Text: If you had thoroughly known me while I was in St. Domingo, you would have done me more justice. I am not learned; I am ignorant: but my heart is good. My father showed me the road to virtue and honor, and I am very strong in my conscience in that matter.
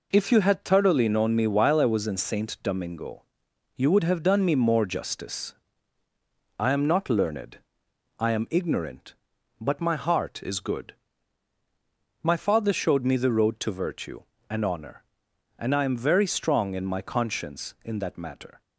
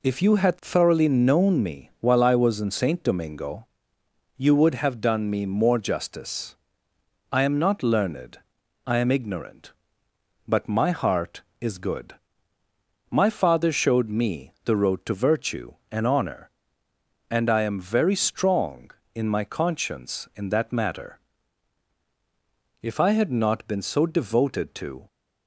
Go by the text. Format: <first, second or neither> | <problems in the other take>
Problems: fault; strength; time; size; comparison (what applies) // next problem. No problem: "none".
first | goes on to say "If I had not been so devoted to"; strong; from 22.8 s on; 2.2 s long